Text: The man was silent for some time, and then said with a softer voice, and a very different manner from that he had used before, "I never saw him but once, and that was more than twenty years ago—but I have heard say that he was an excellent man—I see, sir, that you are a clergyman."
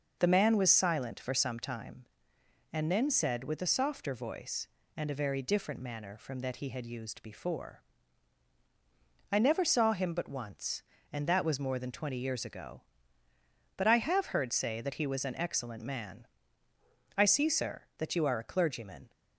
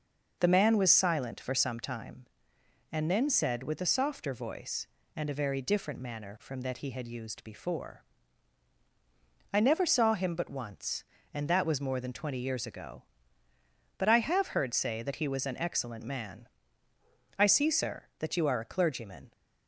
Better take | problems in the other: neither | none

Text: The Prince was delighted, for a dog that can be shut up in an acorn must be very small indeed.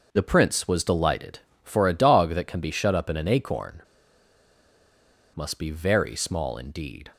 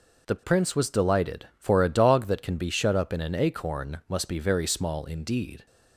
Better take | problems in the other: second | starts louder than the rest; until 1.1 s; 6 dB // pauses between "acorn" and "must"; strong; at 3.8 s; 1.5 s long

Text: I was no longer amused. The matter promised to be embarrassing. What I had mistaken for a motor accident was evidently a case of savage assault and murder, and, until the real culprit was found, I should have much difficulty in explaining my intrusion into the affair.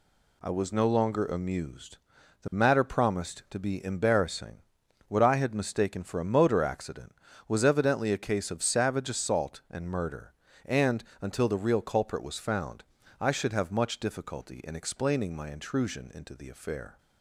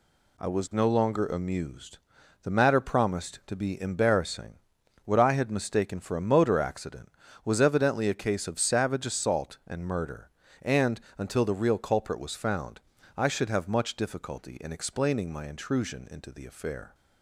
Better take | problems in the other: neither | none

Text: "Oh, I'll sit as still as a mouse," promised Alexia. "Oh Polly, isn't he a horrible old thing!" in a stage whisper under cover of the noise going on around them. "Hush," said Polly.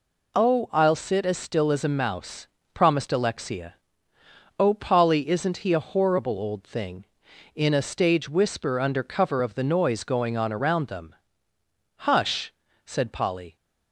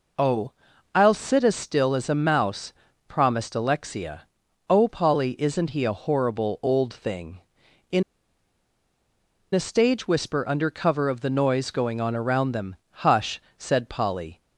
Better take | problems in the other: first | pauses between "in" and "a"; strong; at 8.0 s; 1.5 s long

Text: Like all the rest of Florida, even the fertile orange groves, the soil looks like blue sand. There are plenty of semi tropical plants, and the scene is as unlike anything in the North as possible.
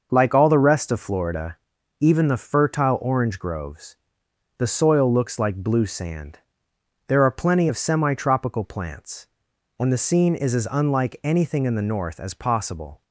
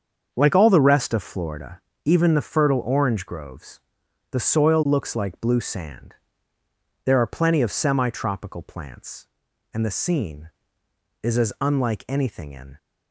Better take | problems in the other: first | starts louder than the rest; until 1.3 s; 7 dB; noticeable in the first // stops before "the North as possible"; at 12.7 s

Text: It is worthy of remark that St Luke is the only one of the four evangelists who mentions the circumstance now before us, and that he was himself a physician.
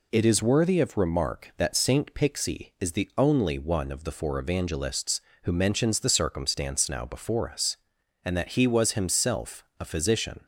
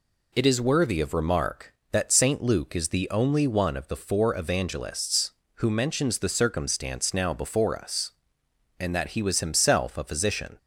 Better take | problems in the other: second | says "Pixie" for "Luke"; at 2.1 s // pauses between "himself" and "a"; slight; at 9.6 s; 0.16 s long

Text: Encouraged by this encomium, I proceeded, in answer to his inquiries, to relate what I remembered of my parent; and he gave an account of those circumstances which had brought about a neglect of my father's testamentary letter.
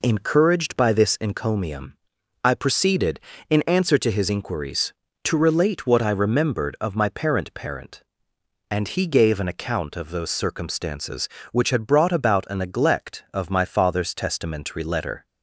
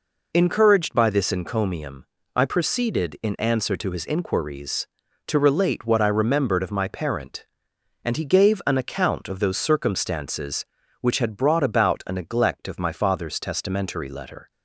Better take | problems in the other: second | says "parent" twice; at 7.5 s

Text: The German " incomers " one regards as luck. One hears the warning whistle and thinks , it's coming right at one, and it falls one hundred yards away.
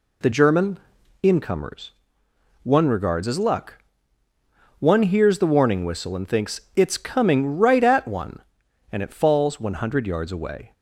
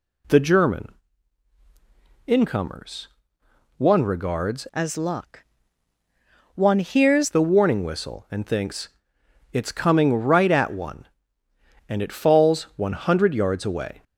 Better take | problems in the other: first | changes voice from "as" to "hears"; from 4.7 to 7.2 s; 2.5 s long

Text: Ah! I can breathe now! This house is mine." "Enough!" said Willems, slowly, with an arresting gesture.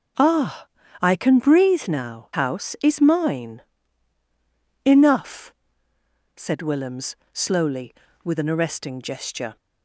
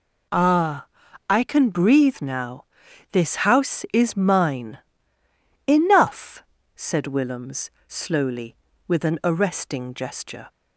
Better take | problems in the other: second | skips "This"; at 2.3 s

